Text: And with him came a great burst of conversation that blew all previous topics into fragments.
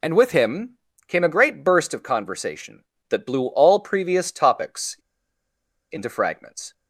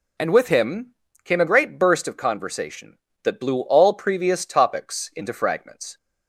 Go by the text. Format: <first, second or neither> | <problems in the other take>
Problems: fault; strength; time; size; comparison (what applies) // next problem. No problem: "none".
second | pauses between "him" and "came"; slight; at 0.7 s; 0.30 s long; slight in the second // pauses between "topics" and "into"; noticeable; at 4.9 s; 0.94 s long